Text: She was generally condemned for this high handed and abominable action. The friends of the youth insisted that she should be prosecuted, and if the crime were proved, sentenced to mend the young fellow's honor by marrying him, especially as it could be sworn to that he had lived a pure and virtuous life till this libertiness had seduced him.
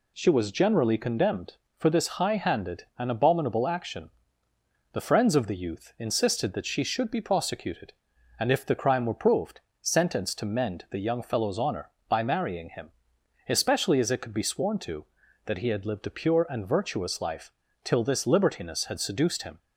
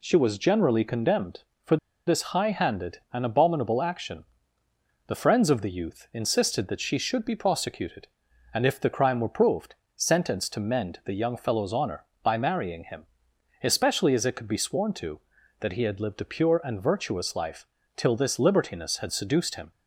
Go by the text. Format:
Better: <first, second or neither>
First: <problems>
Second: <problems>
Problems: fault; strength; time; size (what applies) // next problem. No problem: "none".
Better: first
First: pauses between "life" and "till"; slight; at 17.5 s; 0.32 s long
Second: pauses between "for" and "this"; slight; at 1.7 s; 0.30 s long // pauses between "life" and "till"; slight; at 17.6 s; 0.30 s long